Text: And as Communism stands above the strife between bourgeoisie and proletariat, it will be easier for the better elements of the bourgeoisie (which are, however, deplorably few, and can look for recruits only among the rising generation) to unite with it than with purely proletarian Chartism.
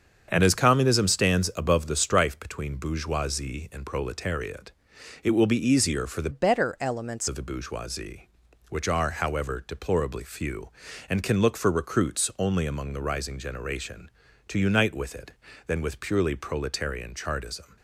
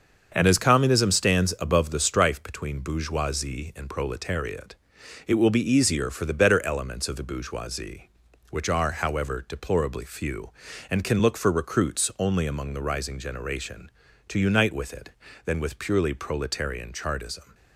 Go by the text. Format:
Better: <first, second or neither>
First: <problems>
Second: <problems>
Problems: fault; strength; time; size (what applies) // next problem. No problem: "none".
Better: second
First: starts louder than the rest; strong; until 1.3 s; 7 dB // changes voice from "better" to "elements"; from 6.3 to 7.2 s; 0.9 s long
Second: starts louder than the rest; until 1.3 s; 6.5 dB